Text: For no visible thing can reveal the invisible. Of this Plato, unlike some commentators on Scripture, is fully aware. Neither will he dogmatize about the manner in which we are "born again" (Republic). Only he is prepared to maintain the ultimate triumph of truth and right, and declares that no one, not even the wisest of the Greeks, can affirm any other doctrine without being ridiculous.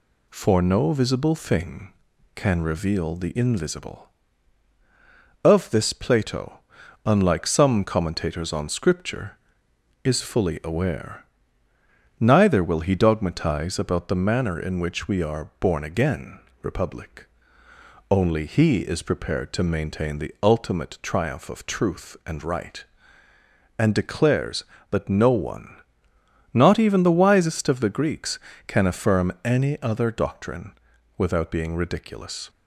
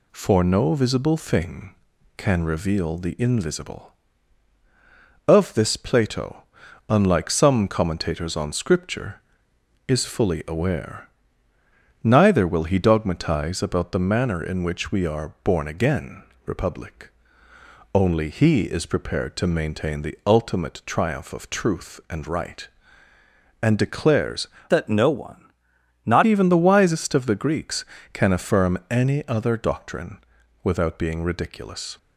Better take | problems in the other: first | changes voice from "that" to "not"; from 24.6 to 26.2 s; 1.6 s long // pauses between "doctrine" and "without"; noticeable; at 30.1 s; 0.46 s long; noticeable in the first

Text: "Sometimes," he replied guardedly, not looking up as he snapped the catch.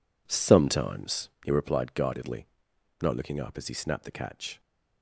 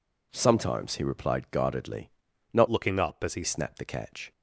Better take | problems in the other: first | changes voice from "looking" to "he"; from 2.6 to 3.4 s; 0.8 s long

